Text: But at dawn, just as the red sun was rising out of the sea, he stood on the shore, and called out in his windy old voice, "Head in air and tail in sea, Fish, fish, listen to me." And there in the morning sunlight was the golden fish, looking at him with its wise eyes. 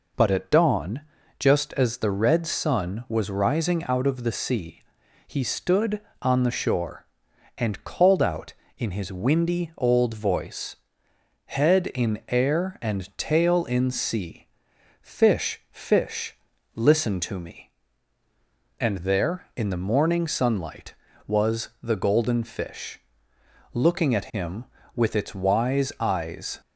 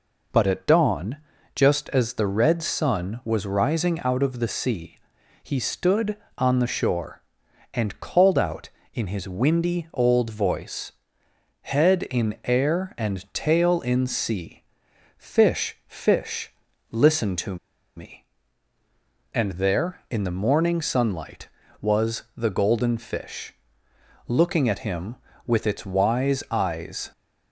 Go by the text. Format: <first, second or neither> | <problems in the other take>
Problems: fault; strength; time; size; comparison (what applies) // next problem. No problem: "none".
first | pauses between "to" and "me"; at 17.5 s; 0.41 s long